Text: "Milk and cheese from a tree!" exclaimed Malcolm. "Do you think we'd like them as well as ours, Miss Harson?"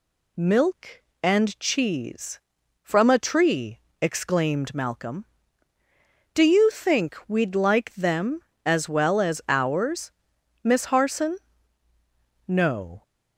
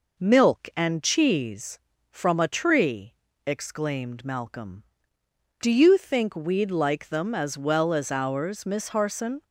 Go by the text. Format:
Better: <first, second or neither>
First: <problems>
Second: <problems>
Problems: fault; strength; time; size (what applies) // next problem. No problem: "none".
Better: second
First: goes on to say "No"; from 12.4 s on; 0.54 s long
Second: none